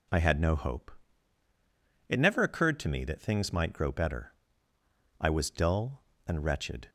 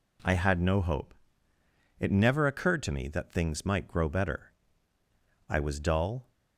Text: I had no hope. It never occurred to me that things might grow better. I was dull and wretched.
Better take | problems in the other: first | stops before "and wretched"; at 6.3 s

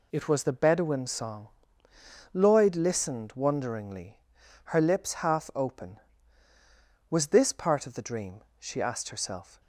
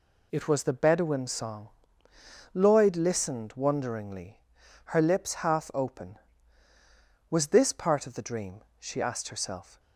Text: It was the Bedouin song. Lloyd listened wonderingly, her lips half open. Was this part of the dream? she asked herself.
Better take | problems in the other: neither | none

